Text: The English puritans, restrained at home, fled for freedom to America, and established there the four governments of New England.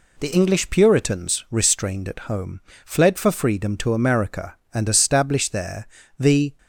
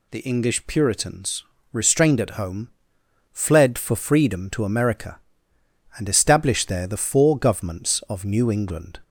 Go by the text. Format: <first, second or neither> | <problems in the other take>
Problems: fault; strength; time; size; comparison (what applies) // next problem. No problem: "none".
second | pauses between "there" and "the"; slight; at 5.8 s; 0.30 s long // stops before "four governments of New England"; at 6.5 s